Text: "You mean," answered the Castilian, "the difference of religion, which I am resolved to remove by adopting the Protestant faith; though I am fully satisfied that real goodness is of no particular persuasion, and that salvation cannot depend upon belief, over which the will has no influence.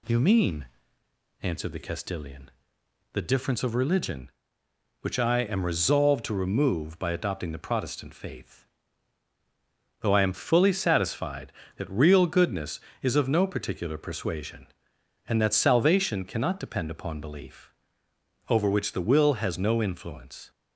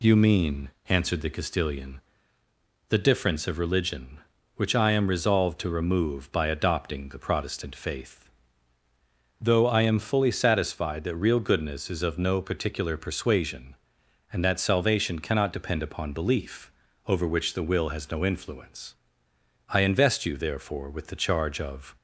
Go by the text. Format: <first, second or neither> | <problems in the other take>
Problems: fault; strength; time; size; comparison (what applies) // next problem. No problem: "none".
first | goes on to say "I invest you therefore with the charge of"; strong; from 19.6 s on; 2.2 s long